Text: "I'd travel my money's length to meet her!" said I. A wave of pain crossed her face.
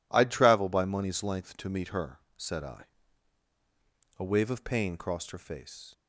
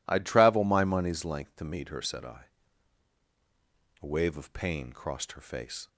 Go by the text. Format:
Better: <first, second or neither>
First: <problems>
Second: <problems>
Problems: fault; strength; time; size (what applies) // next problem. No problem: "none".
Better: second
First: says "by" for "my"; at 0.6 s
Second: none